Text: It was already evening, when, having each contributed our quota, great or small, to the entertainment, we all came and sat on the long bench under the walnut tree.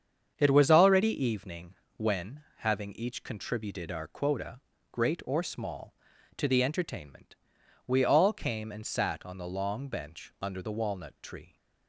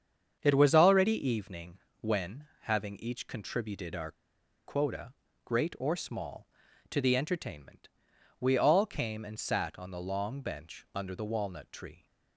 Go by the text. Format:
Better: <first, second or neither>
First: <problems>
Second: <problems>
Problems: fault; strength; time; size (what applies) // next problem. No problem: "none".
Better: first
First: starts louder than the rest; strong; until 1.3 s; 7.5 dB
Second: starts louder than the rest; strong; until 1.4 s; 7.5 dB // pauses between "our" and "quota"; noticeable; at 4.1 s; 0.52 s long